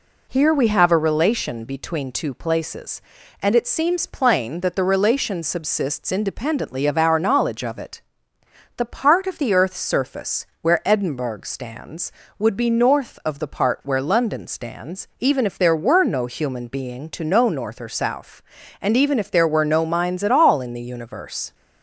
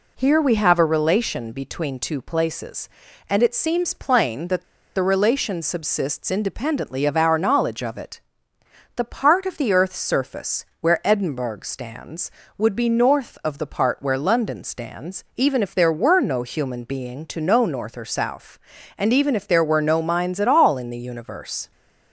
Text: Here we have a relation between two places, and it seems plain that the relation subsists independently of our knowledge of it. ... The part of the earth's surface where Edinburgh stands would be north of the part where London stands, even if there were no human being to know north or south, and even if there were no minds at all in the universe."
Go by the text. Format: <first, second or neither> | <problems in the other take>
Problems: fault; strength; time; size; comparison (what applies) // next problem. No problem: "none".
first | pauses between "that" and "the"; slight; at 4.6 s; 0.32 s long